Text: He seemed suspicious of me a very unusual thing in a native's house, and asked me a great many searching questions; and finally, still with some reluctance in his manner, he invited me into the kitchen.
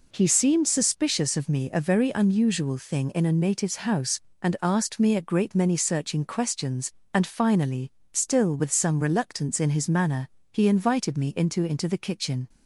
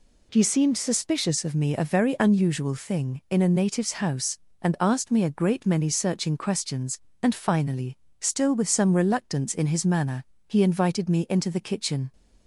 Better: second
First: says "into" twice; at 11.6 s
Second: none

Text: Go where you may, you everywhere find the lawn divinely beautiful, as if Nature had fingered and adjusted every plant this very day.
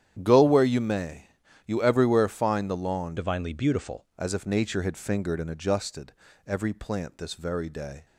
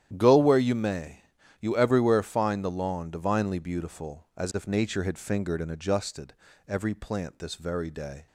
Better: second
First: starts louder than the rest; strong; until 1.2 s; 10 dB // changes voice from "divinely" to "beautiful"; from 3.1 to 4.0 s; 0.9 s long // pauses between "adjusted" and "every"; slight; at 6.1 s; 0.34 s long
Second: starts louder than the rest; strong; until 1.1 s; 10.5 dB // pauses between "adjusted" and "every"; slight; at 6.3 s; 0.34 s long

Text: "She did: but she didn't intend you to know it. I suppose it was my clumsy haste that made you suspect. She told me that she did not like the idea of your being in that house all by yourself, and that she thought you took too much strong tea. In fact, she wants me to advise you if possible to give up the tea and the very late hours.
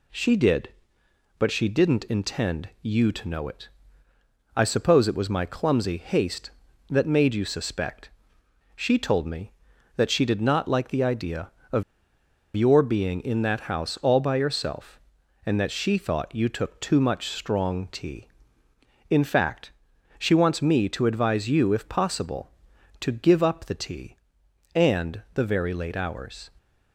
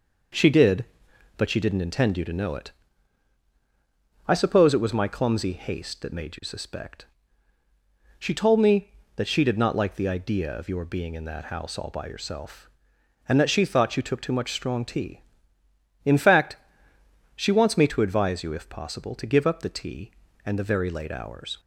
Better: second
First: pauses between "of" and "your"; noticeable; at 11.8 s; 0.71 s long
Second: none

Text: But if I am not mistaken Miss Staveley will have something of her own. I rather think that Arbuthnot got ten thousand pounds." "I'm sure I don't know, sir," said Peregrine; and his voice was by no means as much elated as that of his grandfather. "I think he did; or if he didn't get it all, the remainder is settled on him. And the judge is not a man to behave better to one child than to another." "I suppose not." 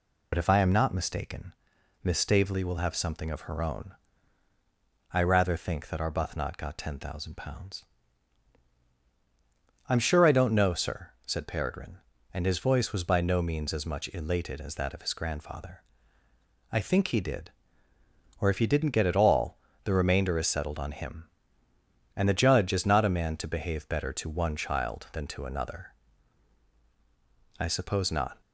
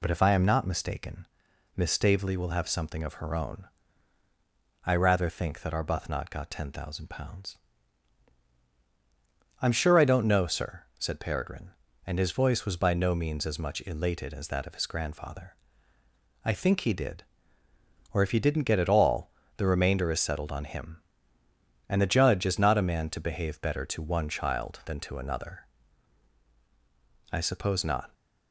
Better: second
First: loses the start of "But"; at 0.3 s; 35 ms // pauses between "mistaken" and "Miss"; noticeable; at 1.5 s; 0.50 s long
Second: pauses between "mistaken" and "Miss"; noticeable; at 1.2 s; 0.50 s long

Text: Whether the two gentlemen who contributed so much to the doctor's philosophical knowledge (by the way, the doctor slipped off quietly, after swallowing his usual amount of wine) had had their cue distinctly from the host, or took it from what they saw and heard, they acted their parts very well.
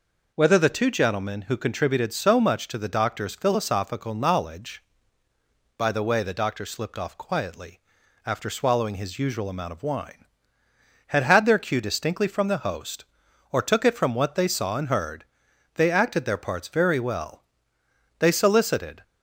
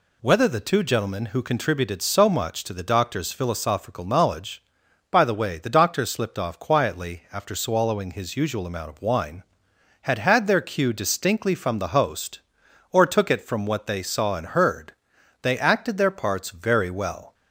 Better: second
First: goes on to say "They solicited"; noticeable; from 18.1 s on; 0.84 s long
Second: none

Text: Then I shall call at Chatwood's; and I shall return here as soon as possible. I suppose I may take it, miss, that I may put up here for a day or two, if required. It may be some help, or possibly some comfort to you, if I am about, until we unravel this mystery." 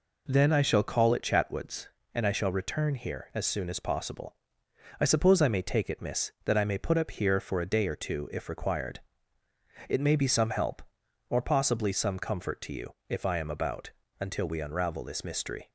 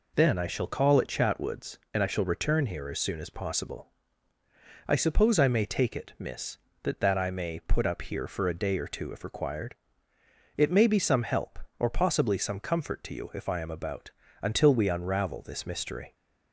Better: first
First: none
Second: says "that" twice; at 7.0 s

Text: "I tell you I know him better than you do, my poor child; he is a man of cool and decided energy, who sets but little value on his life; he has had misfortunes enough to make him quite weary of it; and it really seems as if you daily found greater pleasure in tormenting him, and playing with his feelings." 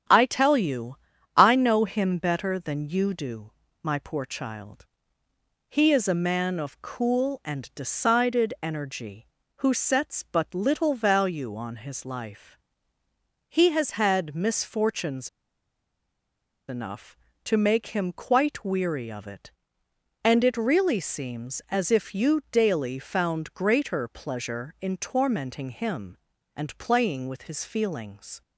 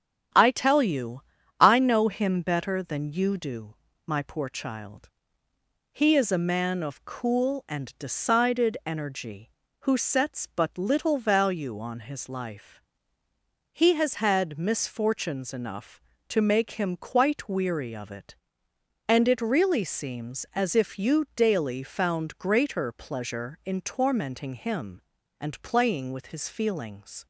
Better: second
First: starts louder than the rest; strong; until 1.4 s; 9 dB // pauses between "you" and "I"; at 0.9 s; 0.38 s long // pauses between "misfortunes" and "enough"; strong; at 15.2 s; 1.3 s long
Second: starts louder than the rest; strong; until 1.7 s; 9 dB // pauses between "you" and "I"; at 1.2 s; 0.36 s long

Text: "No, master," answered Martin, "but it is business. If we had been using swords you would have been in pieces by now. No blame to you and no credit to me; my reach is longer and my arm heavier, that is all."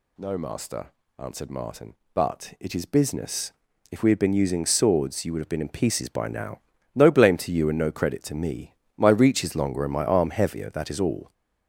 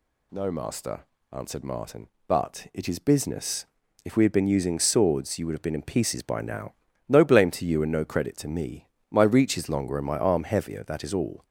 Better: second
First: gets louder; noticeable; throughout; 5.5 dB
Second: none

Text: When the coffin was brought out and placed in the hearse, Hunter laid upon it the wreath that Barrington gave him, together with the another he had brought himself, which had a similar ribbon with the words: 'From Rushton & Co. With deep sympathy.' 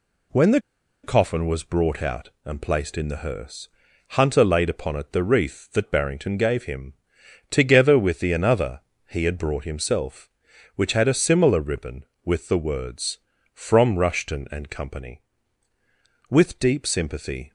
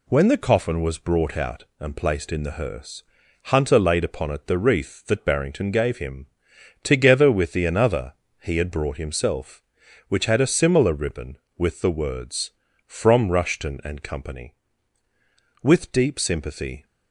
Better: second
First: pauses between "the" and "coffin"; at 0.5 s; 0.43 s long // pauses between "another" and "he"; slight; at 8.7 s; 0.26 s long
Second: pauses between "another" and "he"; slight; at 8.1 s; 0.26 s long

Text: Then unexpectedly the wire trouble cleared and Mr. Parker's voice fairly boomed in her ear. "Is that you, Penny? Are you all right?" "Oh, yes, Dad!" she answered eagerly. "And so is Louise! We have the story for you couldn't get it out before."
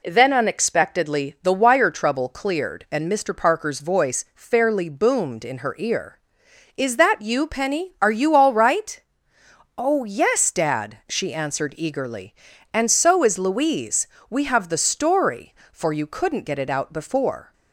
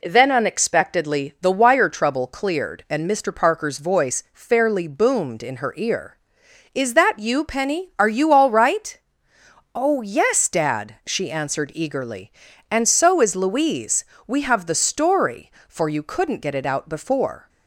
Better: neither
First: none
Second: none

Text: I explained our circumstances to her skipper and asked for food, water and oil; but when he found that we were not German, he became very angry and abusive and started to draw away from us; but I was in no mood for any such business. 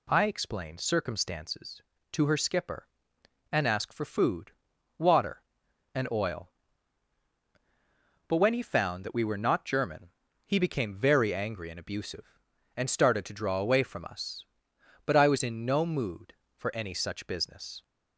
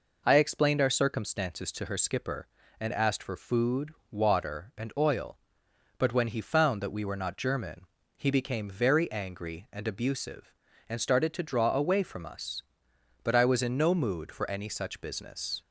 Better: second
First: skips "our"; at 0.8 s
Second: none

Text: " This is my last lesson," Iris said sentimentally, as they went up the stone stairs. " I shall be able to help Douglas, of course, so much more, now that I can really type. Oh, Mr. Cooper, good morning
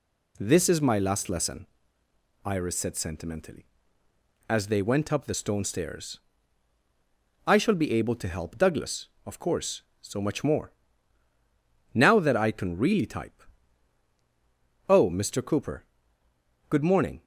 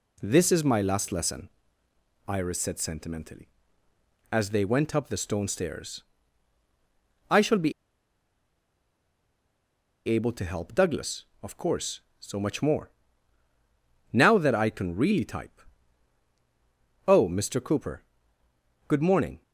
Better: first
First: none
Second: pauses between "be" and "able"; strong; at 7.7 s; 2.3 s long

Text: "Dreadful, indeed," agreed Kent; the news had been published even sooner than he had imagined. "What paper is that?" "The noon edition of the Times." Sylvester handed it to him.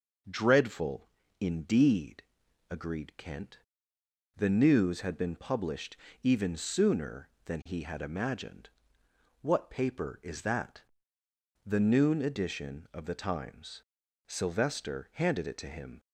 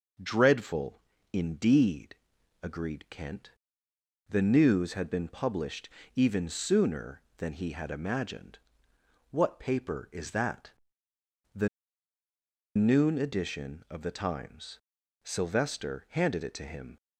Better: first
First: pauses between "published" and "even"; slight; at 5.9 s; 0.26 s long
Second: pauses between "published" and "even"; slight; at 5.8 s; 0.26 s long // pauses between "The" and "noon"; at 11.6 s; 1.0 s long

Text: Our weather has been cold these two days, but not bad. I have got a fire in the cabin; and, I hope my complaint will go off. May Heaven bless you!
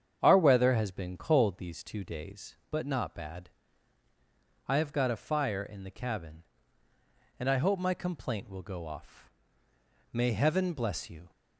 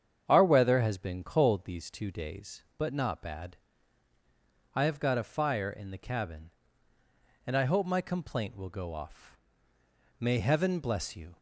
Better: neither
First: starts louder than the rest; strong; until 1.2 s; 8 dB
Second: starts louder than the rest; strong; until 1.2 s; 8 dB

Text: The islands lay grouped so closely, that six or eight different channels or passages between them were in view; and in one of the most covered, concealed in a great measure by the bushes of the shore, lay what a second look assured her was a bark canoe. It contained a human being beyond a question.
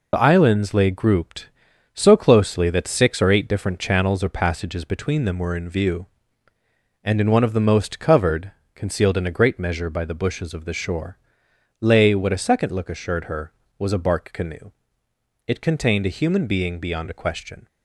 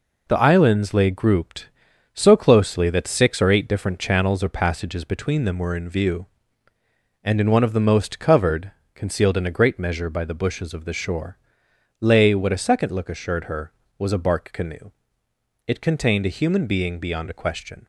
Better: second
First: loses the start of "The"; at 0.1 s; 40 ms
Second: none

